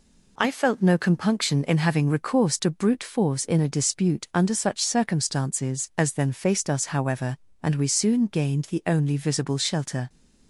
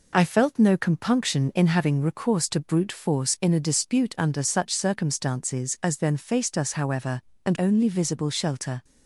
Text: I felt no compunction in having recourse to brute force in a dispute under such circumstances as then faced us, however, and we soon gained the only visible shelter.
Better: first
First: none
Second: skips "we soon gained the"; at 7.5 s

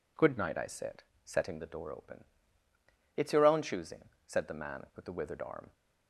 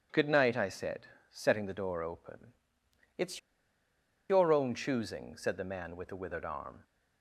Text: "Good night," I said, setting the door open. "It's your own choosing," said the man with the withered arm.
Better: first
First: none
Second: pauses between "It's" and "your"; noticeable; at 3.3 s; 0.91 s long

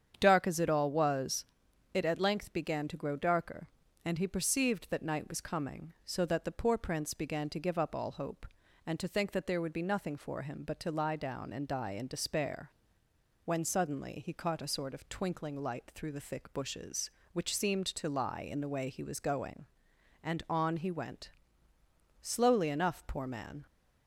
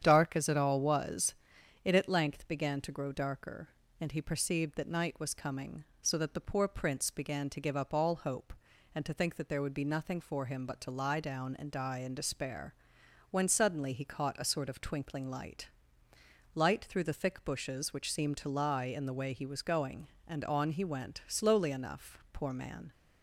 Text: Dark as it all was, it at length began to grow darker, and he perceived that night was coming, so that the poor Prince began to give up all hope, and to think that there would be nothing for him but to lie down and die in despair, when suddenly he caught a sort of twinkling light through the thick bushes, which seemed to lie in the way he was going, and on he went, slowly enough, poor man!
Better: first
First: starts louder than the rest; strong; until 1.2 s; 8 dB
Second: starts louder than the rest; strong; until 1.0 s; 8.5 dB // says "light" twice; at 16.5 s

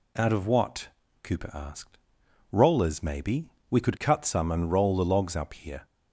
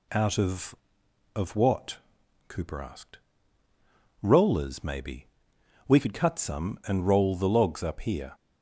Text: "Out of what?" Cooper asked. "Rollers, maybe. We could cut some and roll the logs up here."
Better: first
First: none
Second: says "of" twice; at 1.3 s

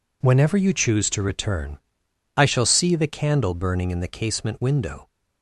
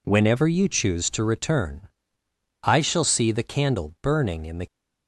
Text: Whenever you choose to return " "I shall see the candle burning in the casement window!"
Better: first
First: none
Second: stops before "casement window"; at 4.6 s

